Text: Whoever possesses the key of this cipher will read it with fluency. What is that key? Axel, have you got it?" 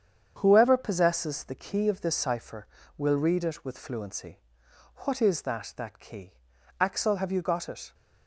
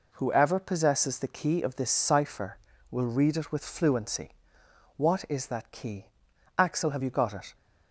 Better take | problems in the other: second | starts louder than the rest; strong; until 1.3 s; 8 dB // says "that" twice; at 5.7 s

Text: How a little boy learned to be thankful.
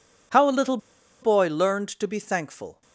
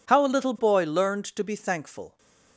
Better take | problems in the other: second | pauses between "little" and "boy"; at 0.7 s; 0.44 s long

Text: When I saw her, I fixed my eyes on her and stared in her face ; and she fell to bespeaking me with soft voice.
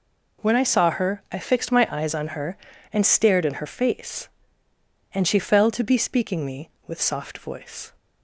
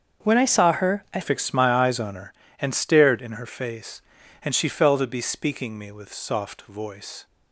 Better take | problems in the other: first | starts louder than the rest; until 1.3 s; 6.5 dB // changes voice at "fixed"; from 1.2 s on; 6.0 s long

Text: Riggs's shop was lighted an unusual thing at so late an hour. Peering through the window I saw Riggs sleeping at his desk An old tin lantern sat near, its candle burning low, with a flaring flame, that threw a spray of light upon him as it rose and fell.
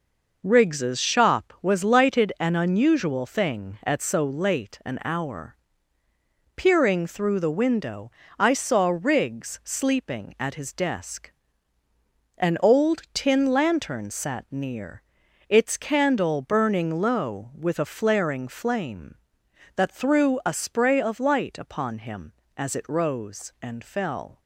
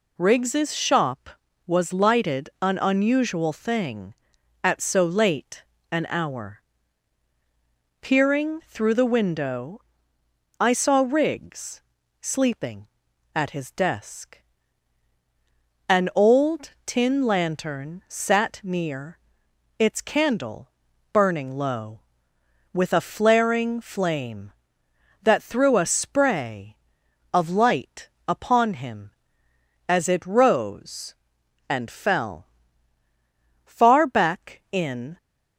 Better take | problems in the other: first | pauses between "late" and "an"; slight; at 5.6 s; 0.28 s long // pauses between "window" and "I"; noticeable; at 9.7 s; 0.80 s long; slight in the first // pauses between "Riggs" and "sleeping"; slight; at 11.8 s; 0.36 s long // pauses between "desk" and "An"; strong; at 14.3 s; 1.4 s long; also in the first // pauses between "old" and "tin"; slight; at 16.7 s; 0.16 s long // pauses between "candle" and "burning"; at 20.7 s; 0.42 s long // pauses between "light" and "upon"; slight; at 28.0 s; 0.18 s long // goes on to say "Far back in"; from 33.6 s on; 1.5 s long

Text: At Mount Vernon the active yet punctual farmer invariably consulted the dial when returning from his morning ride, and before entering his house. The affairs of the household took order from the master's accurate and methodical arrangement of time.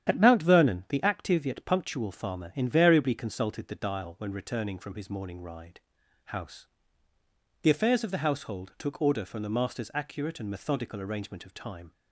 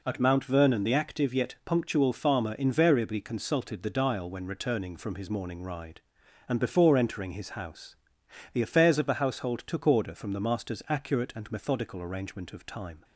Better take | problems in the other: second | starts louder than the rest; strong; until 1.1 s; 10 dB // skips "and before entering his"; at 6.0 s

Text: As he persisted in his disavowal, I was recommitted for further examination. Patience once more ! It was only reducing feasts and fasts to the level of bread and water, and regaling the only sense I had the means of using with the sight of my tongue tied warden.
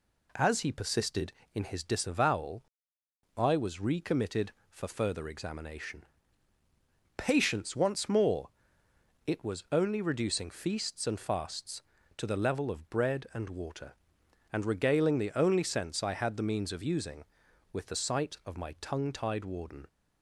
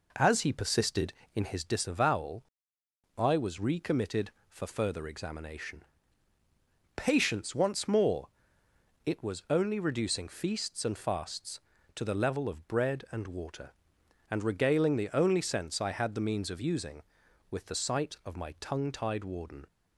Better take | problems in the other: first | starts louder than the rest; noticeable; until 1.7 s; 4 dB

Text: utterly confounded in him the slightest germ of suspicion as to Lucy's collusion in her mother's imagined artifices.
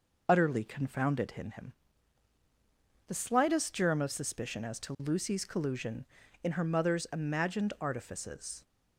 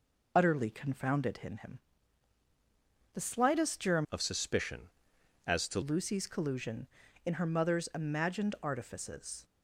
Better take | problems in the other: first | pauses between "him" and "the"; strong; at 1.7 s; 1.3 s long; strong in the first // changes voice from "of" to "to"; from 4.1 to 5.8 s; 1.7 s long

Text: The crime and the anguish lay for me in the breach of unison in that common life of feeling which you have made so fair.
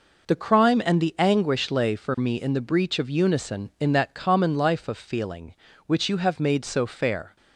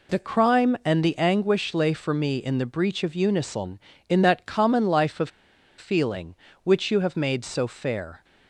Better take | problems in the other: first | pauses between "of" and "feeling"; noticeable; at 5.2 s; 0.49 s long

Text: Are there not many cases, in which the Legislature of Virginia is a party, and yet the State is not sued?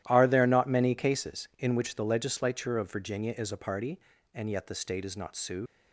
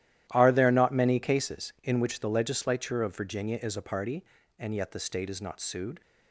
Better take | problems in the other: second | starts louder than the rest; strong; until 1.0 s; 13 dB; strong in the second // leaves "sued" unfinished; at 5.6 s; 105 ms

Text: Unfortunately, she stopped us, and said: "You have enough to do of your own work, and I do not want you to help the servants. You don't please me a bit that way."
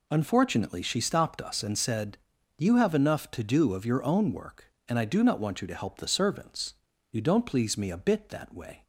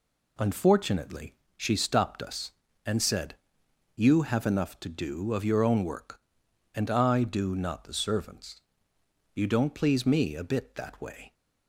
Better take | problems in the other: first | skips "want you to help"; at 7.8 s

